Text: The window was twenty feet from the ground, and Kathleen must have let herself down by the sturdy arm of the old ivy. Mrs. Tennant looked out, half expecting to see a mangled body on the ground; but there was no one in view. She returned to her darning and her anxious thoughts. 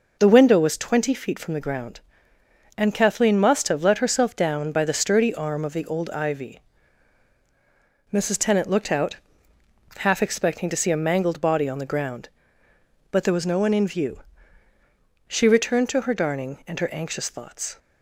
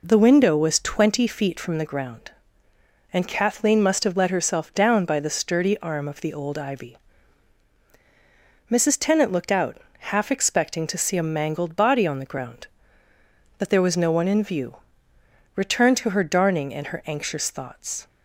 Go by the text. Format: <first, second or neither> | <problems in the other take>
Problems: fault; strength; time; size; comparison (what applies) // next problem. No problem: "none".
first | skips "She"; at 15.1 s